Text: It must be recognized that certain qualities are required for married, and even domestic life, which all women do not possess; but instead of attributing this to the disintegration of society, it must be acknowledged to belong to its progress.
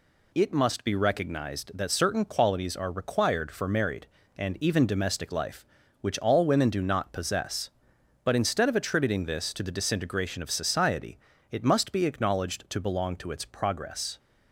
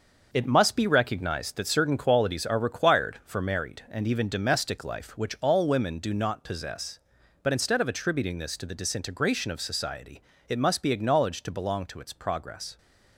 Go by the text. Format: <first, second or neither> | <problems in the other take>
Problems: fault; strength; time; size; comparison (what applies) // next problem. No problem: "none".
first | gets quieter; strong; throughout; 7 dB